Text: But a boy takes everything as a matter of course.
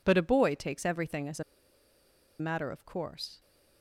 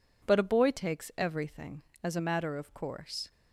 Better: second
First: pauses between "a" and "matter"; noticeable; at 1.4 s; 0.96 s long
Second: none

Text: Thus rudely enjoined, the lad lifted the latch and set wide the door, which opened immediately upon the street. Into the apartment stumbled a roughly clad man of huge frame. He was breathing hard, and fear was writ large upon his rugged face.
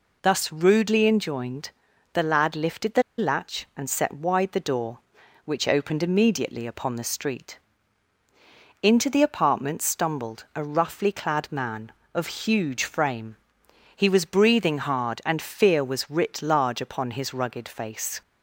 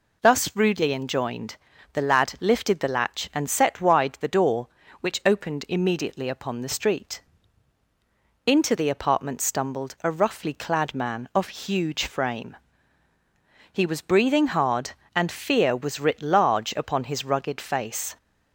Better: second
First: pauses between "the" and "latch"; slight; at 3.0 s; 0.17 s long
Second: none

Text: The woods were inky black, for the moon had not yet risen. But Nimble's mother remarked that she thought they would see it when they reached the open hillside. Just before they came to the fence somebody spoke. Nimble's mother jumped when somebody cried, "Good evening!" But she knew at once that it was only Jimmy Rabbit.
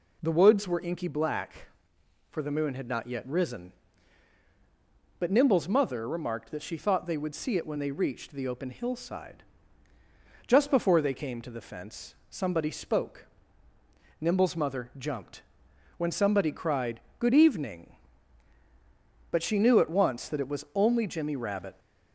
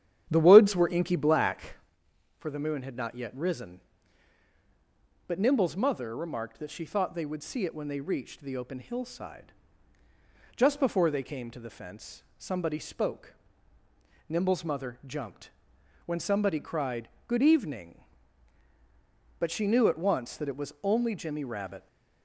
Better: first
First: pauses between "fence" and "somebody"; slight; at 12.1 s; 0.16 s long // pauses between "jumped" and "when"; noticeable; at 15.4 s; 0.54 s long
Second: starts louder than the rest; strong; until 2.0 s; 9.5 dB // pauses between "fence" and "somebody"; slight; at 12.2 s; 0.16 s long // pauses between "jumped" and "when"; noticeable; at 15.5 s; 0.54 s long

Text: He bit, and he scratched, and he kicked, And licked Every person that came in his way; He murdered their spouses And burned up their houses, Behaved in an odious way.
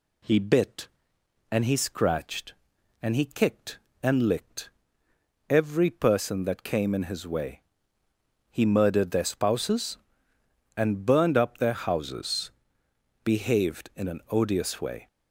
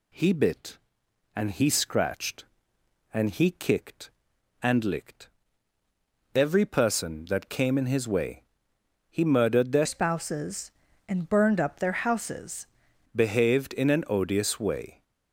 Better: first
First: pauses between "licked" and "Every"; noticeable; at 4.6 s; 0.80 s long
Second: pauses between "licked" and "Every"; at 5.2 s; 1.0 s long // changes voice from "spouses" to "houses"; from 9.8 to 12.6 s; 2.8 s long

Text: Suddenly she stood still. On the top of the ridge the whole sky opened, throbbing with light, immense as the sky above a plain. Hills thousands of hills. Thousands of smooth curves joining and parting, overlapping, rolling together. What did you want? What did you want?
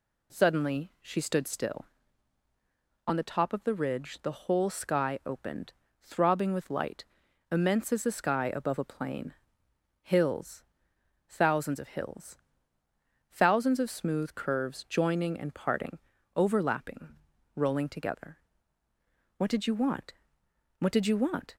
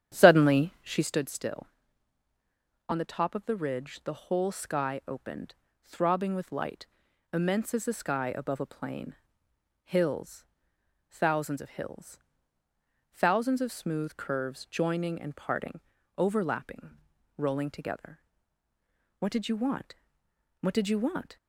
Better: first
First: pauses between "Hills" and "thousands"; noticeable; at 10.6 s; 0.66 s long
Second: starts louder than the rest; strong; until 1.1 s; 9.5 dB // pauses between "Hills" and "thousands"; noticeable; at 10.4 s; 0.66 s long

